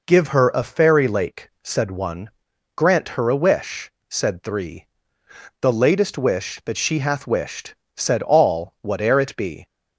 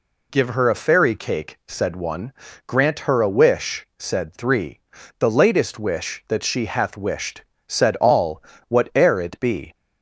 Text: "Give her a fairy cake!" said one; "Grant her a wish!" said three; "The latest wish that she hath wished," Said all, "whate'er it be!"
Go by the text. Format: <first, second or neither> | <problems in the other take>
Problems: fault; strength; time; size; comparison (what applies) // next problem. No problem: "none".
second | says "lake" for "cake"; at 1.0 s